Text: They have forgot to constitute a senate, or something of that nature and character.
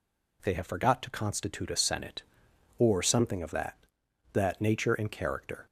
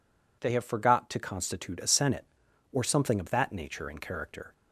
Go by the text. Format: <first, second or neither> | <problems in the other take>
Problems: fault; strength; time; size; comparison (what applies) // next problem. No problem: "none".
second | says "that" twice; at 4.3 s